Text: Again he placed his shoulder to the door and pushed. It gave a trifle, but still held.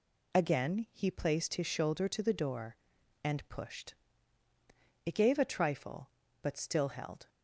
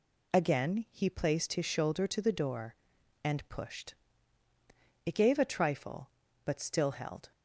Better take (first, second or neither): neither